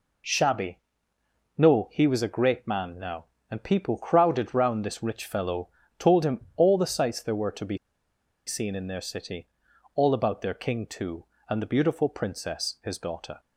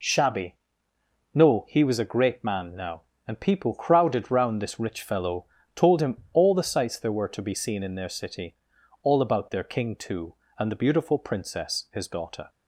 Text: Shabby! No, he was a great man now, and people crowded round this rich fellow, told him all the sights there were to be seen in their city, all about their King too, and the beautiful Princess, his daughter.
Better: second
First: pauses between "be" and "seen"; noticeable; at 7.7 s; 0.69 s long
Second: none

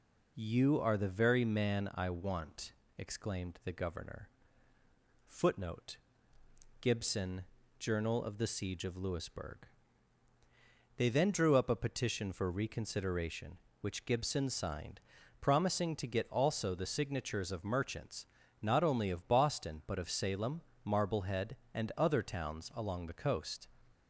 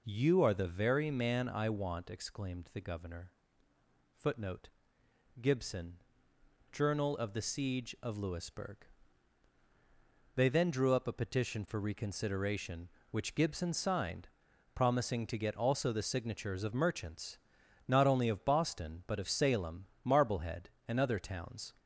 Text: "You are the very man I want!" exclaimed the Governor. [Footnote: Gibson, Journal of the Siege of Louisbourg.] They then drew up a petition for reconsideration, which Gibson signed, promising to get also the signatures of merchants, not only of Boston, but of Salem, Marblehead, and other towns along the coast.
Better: first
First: none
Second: stops before "along the coast"; at 21.7 s

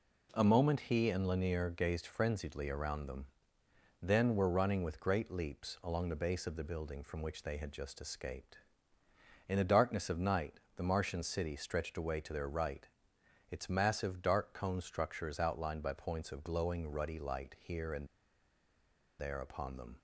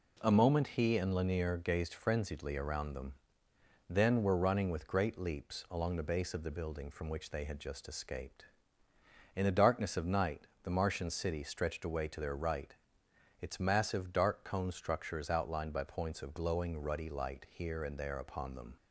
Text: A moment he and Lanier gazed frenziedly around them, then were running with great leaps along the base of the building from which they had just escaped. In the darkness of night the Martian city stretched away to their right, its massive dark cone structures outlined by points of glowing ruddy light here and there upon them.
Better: second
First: pauses between "night" and "the"; slight; at 10.6 s; 0.16 s long // pauses between "and" and "there"; at 18.0 s; 1.1 s long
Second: pauses between "night" and "the"; slight; at 10.4 s; 0.16 s long

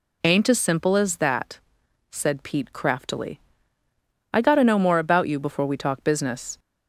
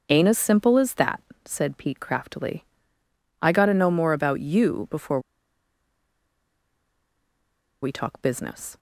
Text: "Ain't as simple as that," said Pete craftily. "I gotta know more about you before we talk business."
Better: first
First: none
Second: starts louder than the rest; until 1.0 s; 6.5 dB // pauses between "before" and "we"; strong; at 5.1 s; 2.6 s long

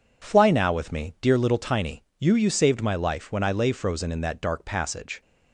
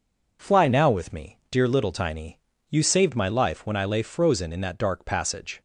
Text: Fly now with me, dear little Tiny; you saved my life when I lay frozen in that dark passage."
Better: second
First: says "you" twice; at 2.3 s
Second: none

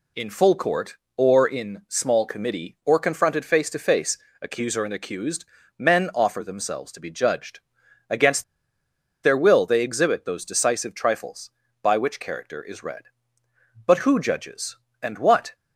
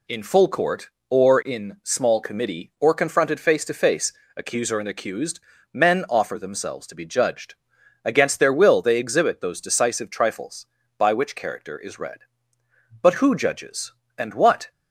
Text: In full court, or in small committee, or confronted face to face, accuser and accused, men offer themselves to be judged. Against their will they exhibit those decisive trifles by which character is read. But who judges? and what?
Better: second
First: pauses between "Against" and "their"; noticeable; at 8.4 s; 0.79 s long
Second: none

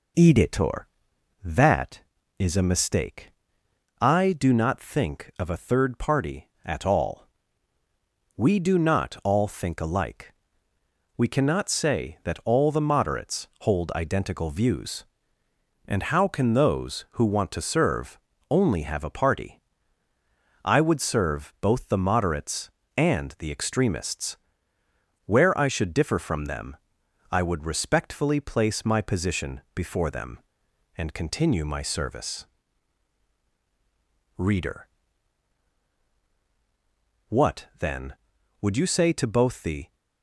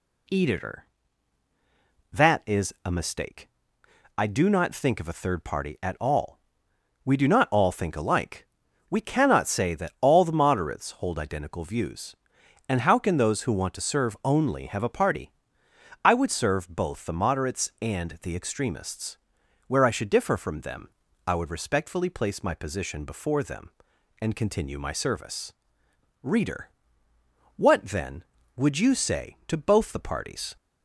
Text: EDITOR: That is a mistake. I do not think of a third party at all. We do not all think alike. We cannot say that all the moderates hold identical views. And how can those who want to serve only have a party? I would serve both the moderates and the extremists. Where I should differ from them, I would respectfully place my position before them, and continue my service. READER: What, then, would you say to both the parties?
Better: second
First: pauses between "serve" and "only"; slight; at 18.1 s; 0.32 s long // stops before "parties"; at 39.9 s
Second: none

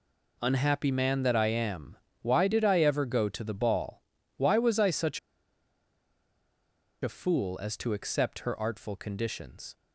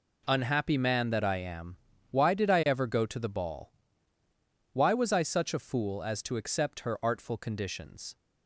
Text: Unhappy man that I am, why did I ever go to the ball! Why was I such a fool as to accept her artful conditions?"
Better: second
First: pauses between "such" and "a"; strong; at 5.1 s; 1.8 s long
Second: none

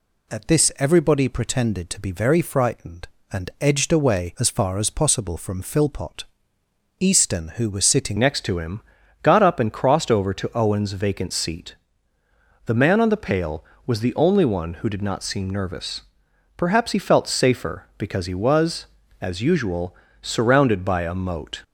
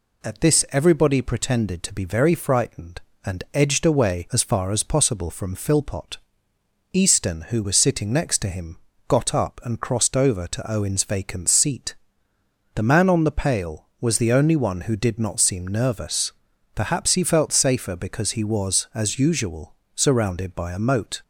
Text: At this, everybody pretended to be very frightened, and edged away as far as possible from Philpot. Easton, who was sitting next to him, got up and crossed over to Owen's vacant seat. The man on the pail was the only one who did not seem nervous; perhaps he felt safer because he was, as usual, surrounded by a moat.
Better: second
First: changes voice at "next"; from 8.1 s on; 13.5 s long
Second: none

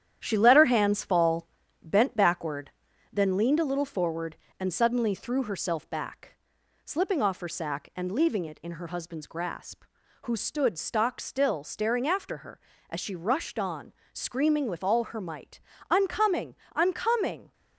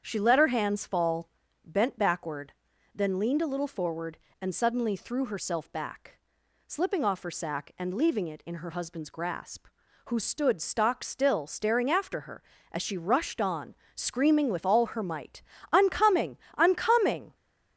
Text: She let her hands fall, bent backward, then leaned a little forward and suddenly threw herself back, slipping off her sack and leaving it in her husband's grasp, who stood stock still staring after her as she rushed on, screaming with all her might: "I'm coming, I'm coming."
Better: second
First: gets quieter; noticeable; throughout; 4 dB // starts louder than the rest; strong; until 1.2 s; 10 dB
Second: starts louder than the rest; strong; until 1.0 s; 8 dB

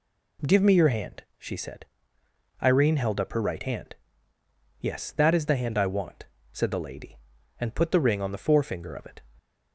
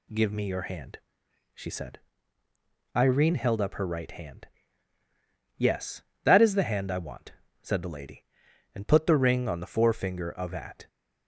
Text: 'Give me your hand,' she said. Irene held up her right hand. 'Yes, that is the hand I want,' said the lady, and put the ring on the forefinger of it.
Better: first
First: none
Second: says "at" for "it"; at 10.5 s

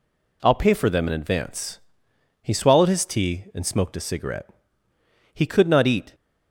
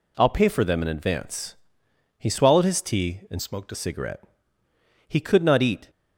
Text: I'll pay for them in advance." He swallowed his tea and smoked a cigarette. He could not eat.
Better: first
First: none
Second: changes voice from "smoked" to "a"; from 3.4 to 3.7 s; 0.3 s long

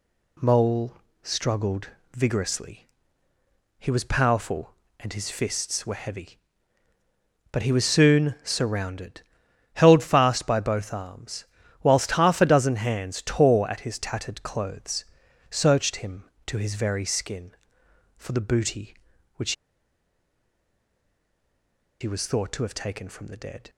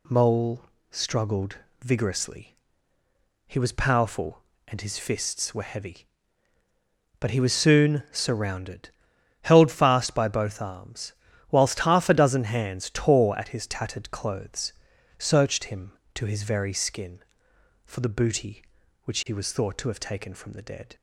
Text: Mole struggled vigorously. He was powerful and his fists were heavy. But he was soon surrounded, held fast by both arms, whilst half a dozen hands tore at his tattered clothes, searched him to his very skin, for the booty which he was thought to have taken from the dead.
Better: second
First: pauses between "Mole" and "struggled"; slight; at 0.9 s; 0.30 s long // pauses between "struggled" and "vigorously"; slight; at 1.8 s; 0.28 s long // pauses between "which" and "he"; strong; at 19.5 s; 2.4 s long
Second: pauses between "Mole" and "struggled"; slight; at 0.6 s; 0.30 s long // pauses between "struggled" and "vigorously"; slight; at 1.5 s; 0.28 s long

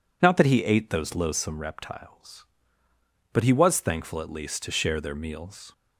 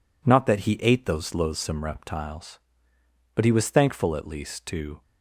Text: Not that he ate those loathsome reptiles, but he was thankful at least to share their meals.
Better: first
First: none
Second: stops before "share their meals"; at 5.0 s

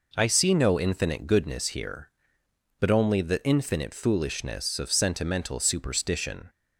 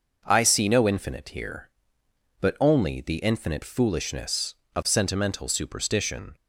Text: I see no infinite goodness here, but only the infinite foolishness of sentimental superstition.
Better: first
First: none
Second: skips "goodness"; at 1.2 s

